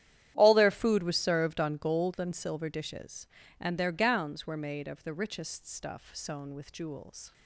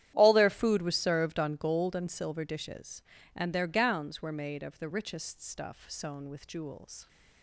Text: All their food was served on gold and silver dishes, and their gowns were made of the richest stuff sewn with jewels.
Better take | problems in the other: neither | starts louder than the rest; strong; the same in both

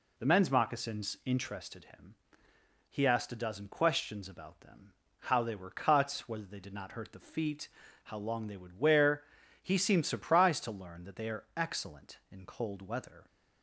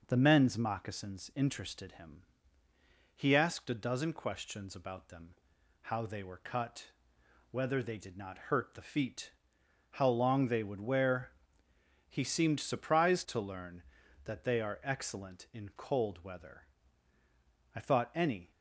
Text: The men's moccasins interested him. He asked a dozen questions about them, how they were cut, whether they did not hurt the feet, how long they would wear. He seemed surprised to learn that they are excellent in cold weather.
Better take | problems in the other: first | goes on to say "I thought ANY"; noticeable; from 17.7 s on; 0.76 s long

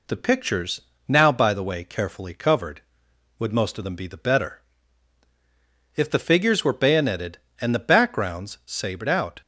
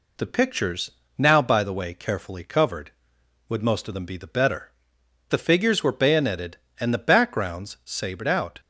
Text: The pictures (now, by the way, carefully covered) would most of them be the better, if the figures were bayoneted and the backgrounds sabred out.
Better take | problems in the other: first | skips "if"; at 5.0 s

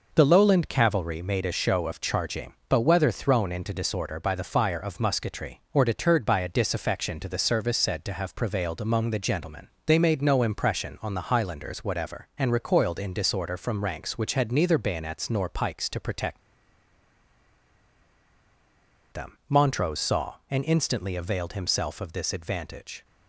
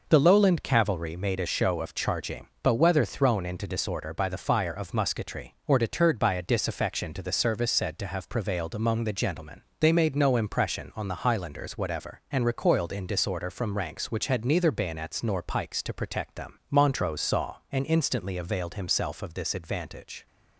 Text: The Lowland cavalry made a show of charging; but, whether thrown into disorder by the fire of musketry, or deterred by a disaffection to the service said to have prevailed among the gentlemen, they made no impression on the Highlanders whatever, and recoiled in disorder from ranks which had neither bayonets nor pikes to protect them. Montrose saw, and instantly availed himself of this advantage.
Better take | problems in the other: second | pauses between "protect" and "them"; strong; at 16.3 s; 2.7 s long

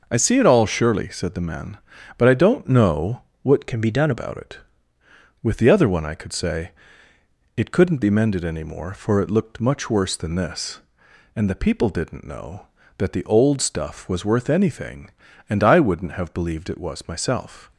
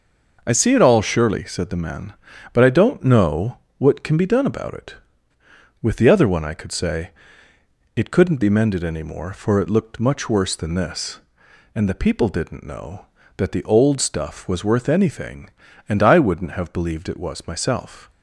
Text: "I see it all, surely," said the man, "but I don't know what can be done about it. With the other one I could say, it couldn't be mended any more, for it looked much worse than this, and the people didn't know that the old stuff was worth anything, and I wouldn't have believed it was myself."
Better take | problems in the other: second | pauses between "know" and "what"; slight; at 3.2 s; 0.20 s long; slight in the second // changes voice from "can" to "done"; from 3.6 to 4.1 s; 0.5 s long

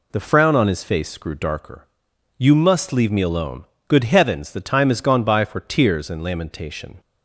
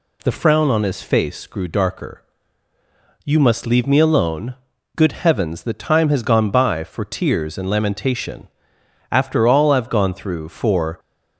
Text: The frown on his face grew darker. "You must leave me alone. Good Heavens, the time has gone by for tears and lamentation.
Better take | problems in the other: first | goes on to say "After all I've gone through for"; strong; from 9.1 s on; 1.8 s long

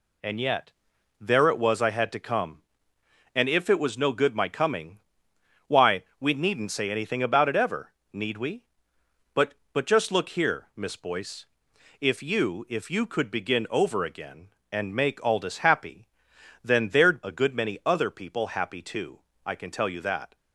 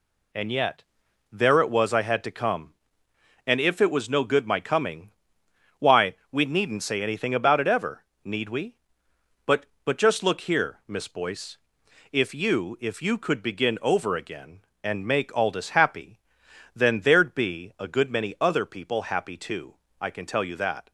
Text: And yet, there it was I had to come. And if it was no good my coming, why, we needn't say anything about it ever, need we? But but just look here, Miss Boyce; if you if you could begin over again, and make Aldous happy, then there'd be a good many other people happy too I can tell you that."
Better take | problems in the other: second | skips "be"; at 17.2 s // pauses between "too" and "I"; slight; at 19.1 s; 0.26 s long; slight in the second

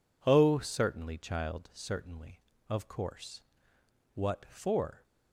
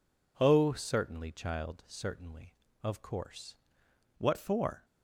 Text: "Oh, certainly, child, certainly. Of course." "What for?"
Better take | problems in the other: first | changes voice at "What"; from 4.1 s on; 0.7 s long

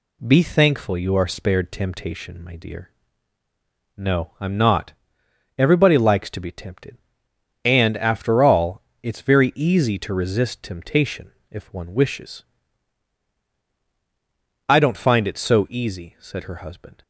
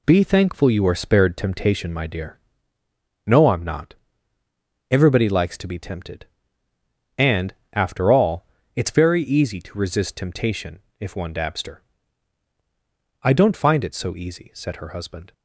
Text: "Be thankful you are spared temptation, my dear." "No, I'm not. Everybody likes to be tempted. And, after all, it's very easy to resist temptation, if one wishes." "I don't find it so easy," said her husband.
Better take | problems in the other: first | says "dabster" for "wishes"; at 11.3 s

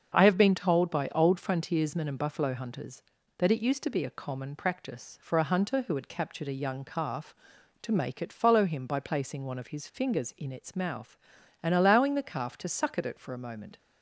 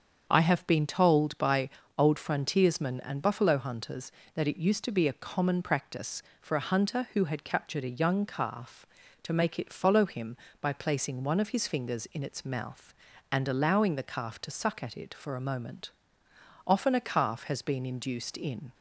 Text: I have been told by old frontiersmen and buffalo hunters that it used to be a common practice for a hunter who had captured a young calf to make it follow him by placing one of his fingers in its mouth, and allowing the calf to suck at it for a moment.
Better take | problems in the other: first | starts louder than the rest; until 1.3 s; 7 dB; also in the first // pauses between "by" and "old"; slight; at 1.6 s; 0.28 s long // goes on to say "Often a calf has been induced in"; strong; from 16.6 s on; 2.0 s long

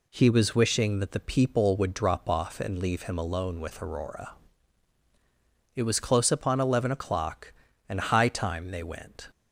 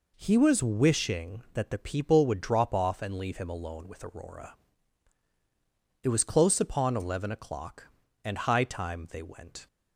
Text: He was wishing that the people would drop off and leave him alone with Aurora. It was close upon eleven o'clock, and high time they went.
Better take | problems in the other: neither | none

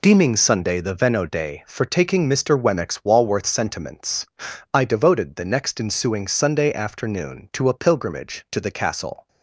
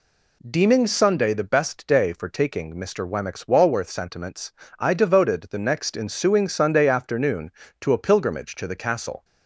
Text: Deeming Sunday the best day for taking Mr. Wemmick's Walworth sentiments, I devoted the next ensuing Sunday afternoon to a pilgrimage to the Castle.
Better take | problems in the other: second | says "veno" for "best"; at 0.9 s

